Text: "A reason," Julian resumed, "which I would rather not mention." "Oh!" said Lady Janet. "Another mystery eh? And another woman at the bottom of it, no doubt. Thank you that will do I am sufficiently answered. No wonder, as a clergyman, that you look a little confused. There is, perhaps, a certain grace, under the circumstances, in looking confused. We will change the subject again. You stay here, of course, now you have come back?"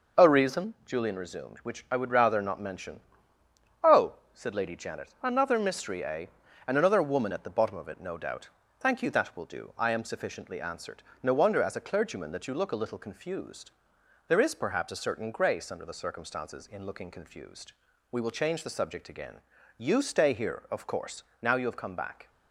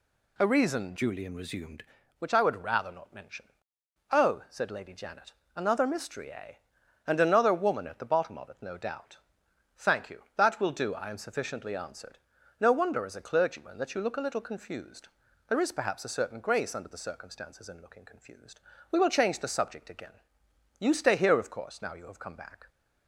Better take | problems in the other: first | changes voice from "Julian" to "resumed"; from 0.9 to 1.8 s; 0.9 s long

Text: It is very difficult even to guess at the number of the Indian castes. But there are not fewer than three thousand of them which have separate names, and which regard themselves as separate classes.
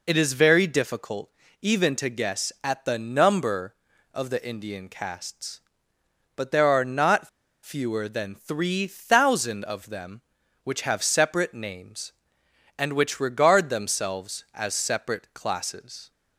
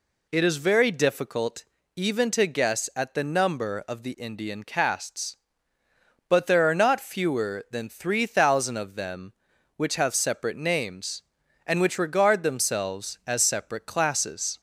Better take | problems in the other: second | pauses between "difficult" and "even"; slight; at 1.2 s; 0.32 s long; slight in the second // pauses between "not" and "fewer"; slight; at 7.2 s; 0.34 s long

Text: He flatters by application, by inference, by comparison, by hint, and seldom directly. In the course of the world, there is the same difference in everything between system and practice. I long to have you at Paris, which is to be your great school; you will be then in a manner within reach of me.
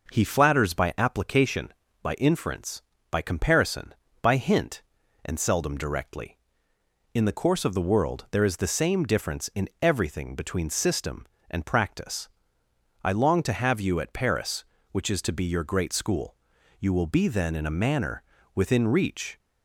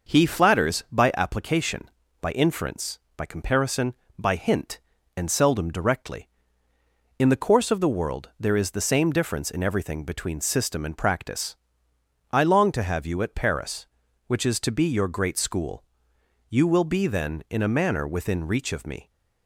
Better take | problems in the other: second | pauses between "manner" and "within"; slight; at 18.2 s; 0.32 s long // stops before "of me"; at 19.3 s

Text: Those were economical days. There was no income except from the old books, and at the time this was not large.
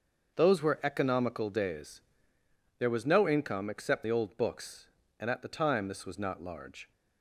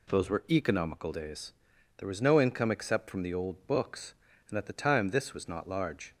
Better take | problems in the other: second | starts louder than the rest; until 1.3 s; 6.5 dB // skips "from"; at 4.0 s

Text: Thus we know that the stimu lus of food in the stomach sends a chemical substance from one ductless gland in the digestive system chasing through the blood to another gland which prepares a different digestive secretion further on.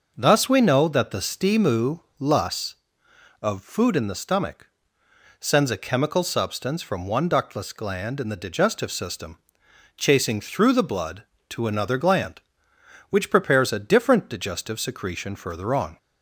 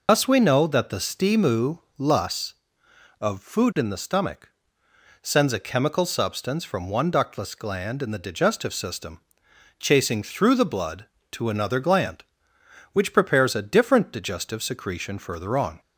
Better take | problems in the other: first | loses the start of "Thus"; at 0.0 s; 145 ms // pauses between "stimu" and "lus"; slight; at 1.7 s; 0.20 s long; slight in the first // pauses between "stomach" and "sends"; noticeable; at 4.5 s; 0.72 s long; noticeable in the first // pauses between "system" and "chasing"; noticeable; at 9.2 s; 0.60 s long; noticeable in the first

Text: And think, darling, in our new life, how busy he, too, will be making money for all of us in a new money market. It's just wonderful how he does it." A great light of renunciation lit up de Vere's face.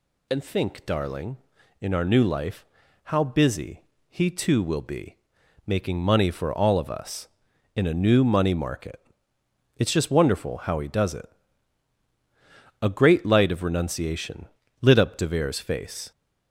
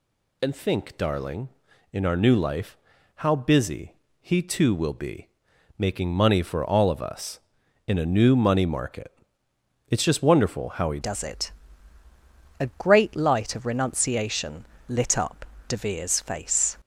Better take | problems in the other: first | pauses between "busy" and "he"; slight; at 3.9 s; 0.28 s long; slight in the first // pauses between "be" and "making"; noticeable; at 5.2 s; 0.50 s long; noticeable in the first // changes voice at "does"; from 11.0 s on; 5.7 s long // pauses between "renunciation" and "lit"; slight; at 14.6 s; 0.24 s long; slight in the first // pauses between "up" and "de"; slight; at 15.4 s; 0.24 s long

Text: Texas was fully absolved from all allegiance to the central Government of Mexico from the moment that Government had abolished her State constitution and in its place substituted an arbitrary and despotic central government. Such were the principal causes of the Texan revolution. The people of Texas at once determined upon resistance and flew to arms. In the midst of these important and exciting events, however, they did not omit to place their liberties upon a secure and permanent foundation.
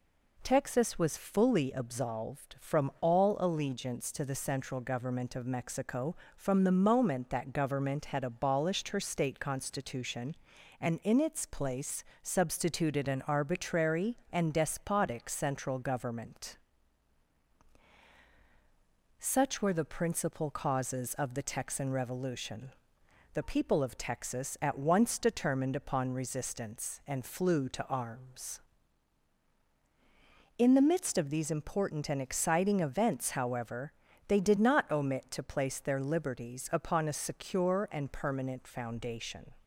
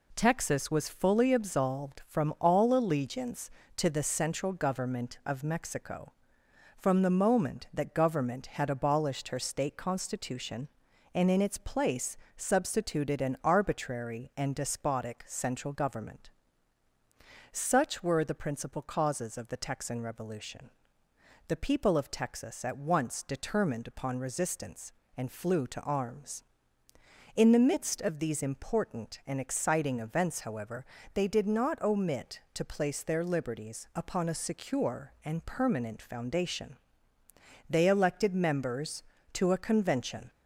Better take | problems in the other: first | pauses between "place" and "substituted"; slight; at 12.1 s; 0.20 s long; slight in the first // goes on to say "They elected members to a convention"; strong; from 37.6 s on; 2.6 s long

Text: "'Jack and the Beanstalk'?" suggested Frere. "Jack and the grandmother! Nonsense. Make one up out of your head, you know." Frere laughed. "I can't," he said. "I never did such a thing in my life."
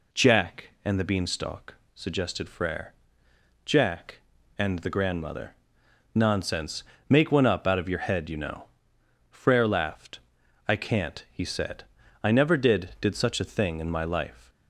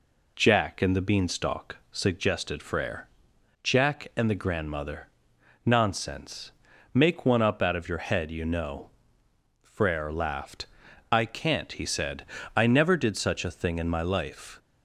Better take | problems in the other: second | says "did" twice; at 12.9 s

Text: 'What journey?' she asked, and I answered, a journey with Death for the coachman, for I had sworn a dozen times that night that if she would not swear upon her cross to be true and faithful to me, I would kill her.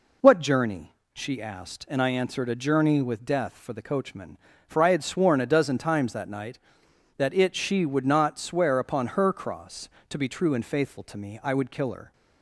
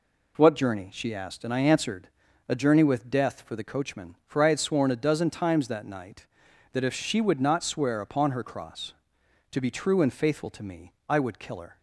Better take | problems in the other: second | says "it" for "if"; at 7.3 s

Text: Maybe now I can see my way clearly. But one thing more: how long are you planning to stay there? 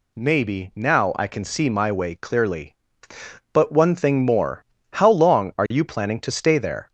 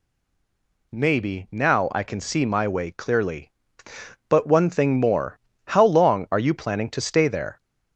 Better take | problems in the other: first | stays silent before the first word; slight; until 0.9 s; 0.9 s long

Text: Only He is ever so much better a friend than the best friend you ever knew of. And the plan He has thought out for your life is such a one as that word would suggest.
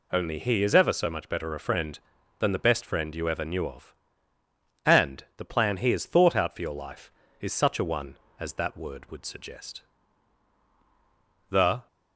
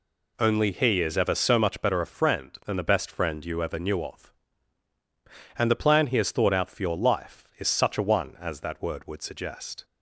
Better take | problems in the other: second | goes on to say "The"; slight; from 11.4 s on; 0.38 s long

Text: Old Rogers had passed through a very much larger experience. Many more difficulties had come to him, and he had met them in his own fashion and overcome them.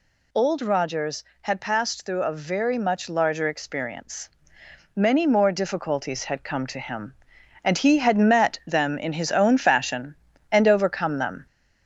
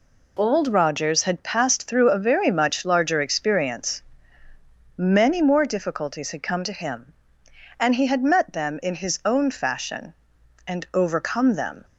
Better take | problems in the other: second | gets louder; slight; throughout; 3.5 dB

